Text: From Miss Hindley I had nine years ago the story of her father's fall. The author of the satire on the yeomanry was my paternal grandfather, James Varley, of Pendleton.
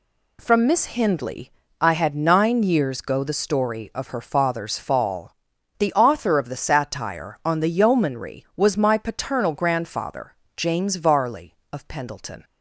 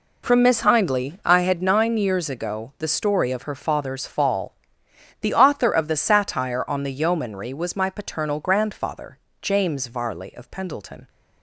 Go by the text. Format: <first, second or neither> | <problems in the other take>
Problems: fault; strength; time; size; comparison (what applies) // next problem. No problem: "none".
second | pauses between "Hindley" and "I"; slight; at 1.5 s; 0.30 s long // says "go" for "ago"; at 3.0 s